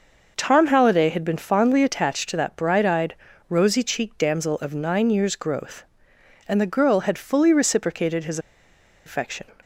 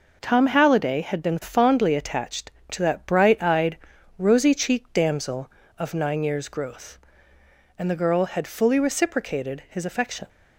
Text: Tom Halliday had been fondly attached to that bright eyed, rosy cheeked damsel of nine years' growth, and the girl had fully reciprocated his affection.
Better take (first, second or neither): second